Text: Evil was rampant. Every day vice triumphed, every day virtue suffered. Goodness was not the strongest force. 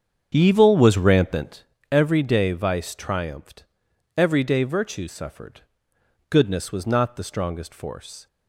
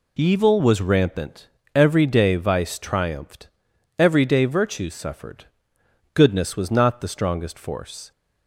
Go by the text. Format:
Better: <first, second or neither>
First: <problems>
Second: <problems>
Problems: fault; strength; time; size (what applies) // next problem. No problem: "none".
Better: second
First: starts louder than the rest; strong; until 1.6 s; 7.5 dB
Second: none